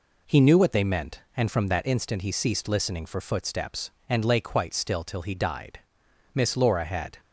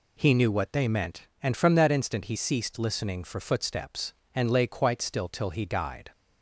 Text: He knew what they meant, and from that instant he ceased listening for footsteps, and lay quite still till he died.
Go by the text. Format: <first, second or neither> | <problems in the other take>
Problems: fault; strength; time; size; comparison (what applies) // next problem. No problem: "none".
second | goes on to say "Miss Laura had"; noticeable; from 6.3 s on; 0.84 s long